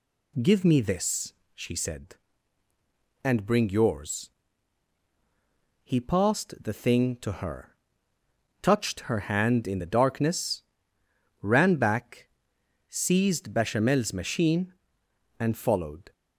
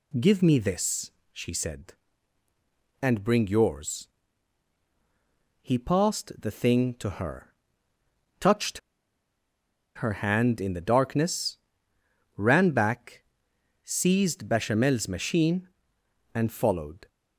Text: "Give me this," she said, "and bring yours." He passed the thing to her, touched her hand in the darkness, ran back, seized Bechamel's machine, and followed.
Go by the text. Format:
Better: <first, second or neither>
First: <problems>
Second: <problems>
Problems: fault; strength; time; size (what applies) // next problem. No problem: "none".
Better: first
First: none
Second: pauses between "touched" and "her"; at 8.7 s; 1.1 s long